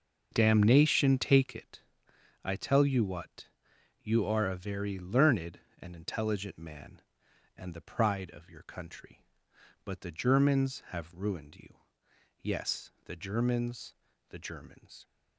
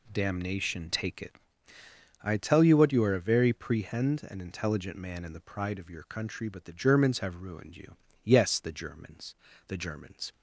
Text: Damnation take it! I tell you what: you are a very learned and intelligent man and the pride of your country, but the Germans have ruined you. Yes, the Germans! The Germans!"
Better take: first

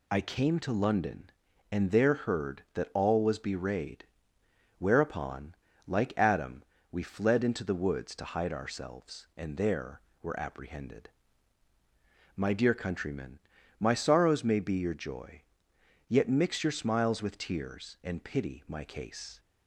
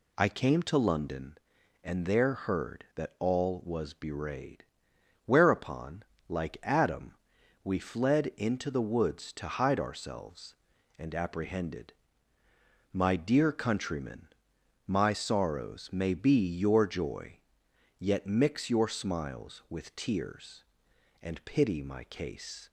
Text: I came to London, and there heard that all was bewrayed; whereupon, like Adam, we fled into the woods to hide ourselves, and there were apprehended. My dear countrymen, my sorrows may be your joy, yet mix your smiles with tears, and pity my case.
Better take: first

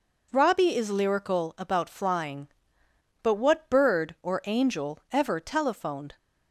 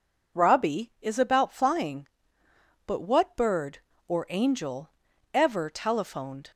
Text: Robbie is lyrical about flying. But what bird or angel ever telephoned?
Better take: first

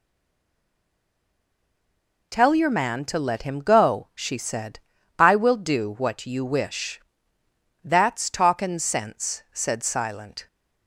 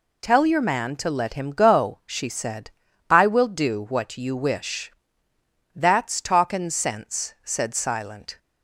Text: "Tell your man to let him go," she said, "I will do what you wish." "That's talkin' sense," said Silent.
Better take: second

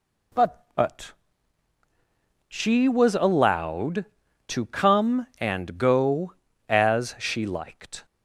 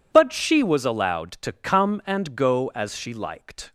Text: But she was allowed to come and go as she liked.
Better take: second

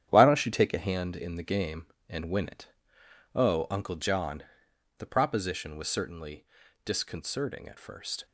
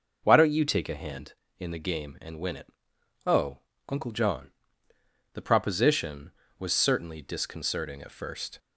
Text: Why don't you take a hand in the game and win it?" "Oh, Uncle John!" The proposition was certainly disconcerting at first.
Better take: second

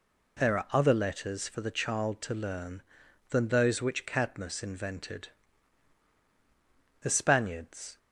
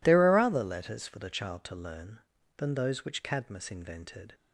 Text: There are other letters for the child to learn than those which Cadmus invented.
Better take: second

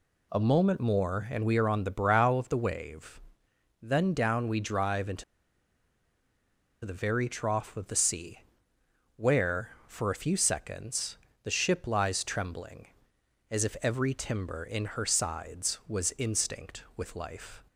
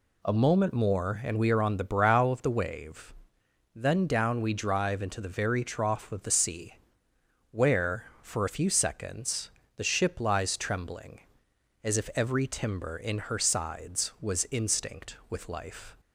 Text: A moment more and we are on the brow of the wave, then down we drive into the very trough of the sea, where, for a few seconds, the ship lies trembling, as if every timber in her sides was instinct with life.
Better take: second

